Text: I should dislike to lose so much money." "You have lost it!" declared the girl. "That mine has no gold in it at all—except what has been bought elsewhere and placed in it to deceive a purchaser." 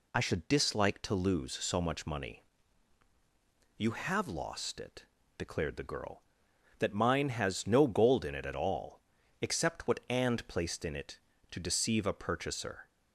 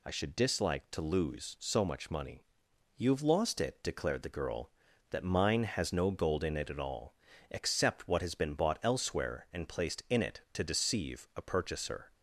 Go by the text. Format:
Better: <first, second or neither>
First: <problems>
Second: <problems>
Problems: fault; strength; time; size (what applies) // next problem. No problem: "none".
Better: second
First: skips "has been bought elsewhere"; at 10.0 s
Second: none